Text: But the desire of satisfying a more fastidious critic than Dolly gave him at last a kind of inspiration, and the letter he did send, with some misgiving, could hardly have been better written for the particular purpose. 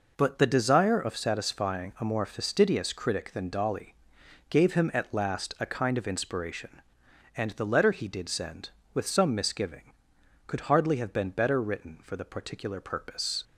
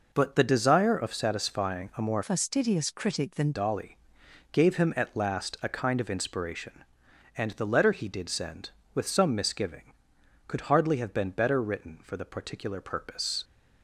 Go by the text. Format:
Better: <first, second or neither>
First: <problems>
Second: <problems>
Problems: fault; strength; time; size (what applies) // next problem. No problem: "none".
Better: first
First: pauses between "Dolly" and "gave"; noticeable; at 3.9 s; 0.54 s long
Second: changes voice from "fastidious" to "than"; from 2.2 to 3.5 s; 1.3 s long // pauses between "Dolly" and "gave"; noticeable; at 3.9 s; 0.54 s long